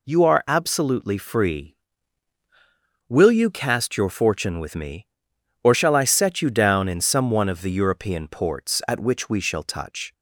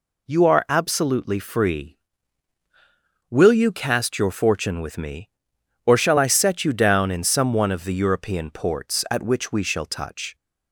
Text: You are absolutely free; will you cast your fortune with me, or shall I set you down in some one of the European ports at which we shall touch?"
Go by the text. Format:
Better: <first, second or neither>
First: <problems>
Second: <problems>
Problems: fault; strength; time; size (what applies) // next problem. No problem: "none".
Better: neither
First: none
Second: none